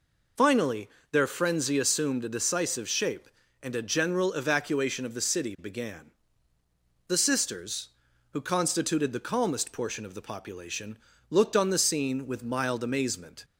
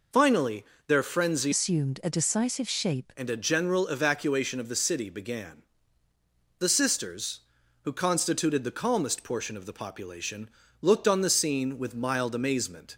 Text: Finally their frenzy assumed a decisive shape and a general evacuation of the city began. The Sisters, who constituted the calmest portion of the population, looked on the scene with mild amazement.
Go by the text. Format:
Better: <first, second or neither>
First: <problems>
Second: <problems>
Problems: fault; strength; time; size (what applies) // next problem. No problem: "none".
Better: first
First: pauses between "Finally" and "their"; slight; at 0.8 s; 0.22 s long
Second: pauses between "Finally" and "their"; slight; at 0.6 s; 0.22 s long // changes voice from "assumed" to "shape"; from 1.5 to 3.1 s; 1.6 s long